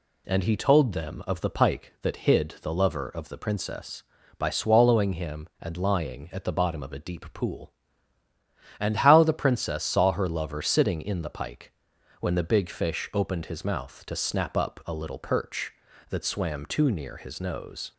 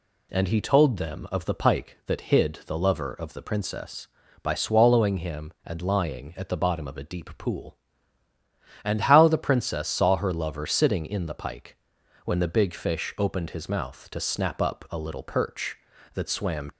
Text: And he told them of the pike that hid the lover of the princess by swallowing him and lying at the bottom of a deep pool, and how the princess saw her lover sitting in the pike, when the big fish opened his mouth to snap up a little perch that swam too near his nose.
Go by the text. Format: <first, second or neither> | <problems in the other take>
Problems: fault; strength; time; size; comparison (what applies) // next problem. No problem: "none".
first | stops before "too near his nose"; at 16.7 s